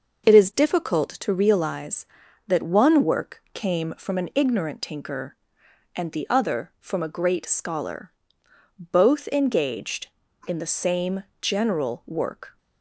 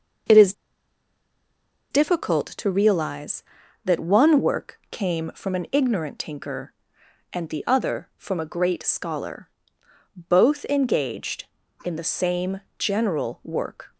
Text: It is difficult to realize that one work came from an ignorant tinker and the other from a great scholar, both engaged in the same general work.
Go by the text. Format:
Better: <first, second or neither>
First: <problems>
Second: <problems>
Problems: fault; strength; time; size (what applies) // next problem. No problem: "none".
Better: first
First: pauses between "same" and "general"; slight; at 11.2 s; 0.18 s long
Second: pauses between "is" and "difficult"; strong; at 0.5 s; 1.3 s long // pauses between "same" and "general"; slight; at 12.6 s; 0.18 s long